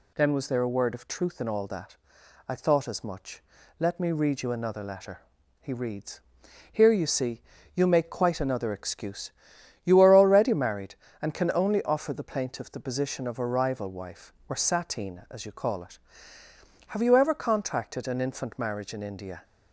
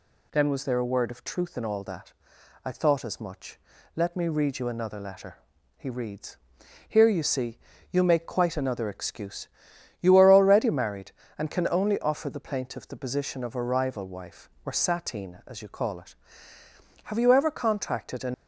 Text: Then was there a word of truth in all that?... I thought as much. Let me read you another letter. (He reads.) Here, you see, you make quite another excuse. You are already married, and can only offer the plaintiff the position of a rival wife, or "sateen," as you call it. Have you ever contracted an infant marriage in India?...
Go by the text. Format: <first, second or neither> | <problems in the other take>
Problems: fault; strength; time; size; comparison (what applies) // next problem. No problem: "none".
first | stops before "infant marriage in India"; at 18.3 s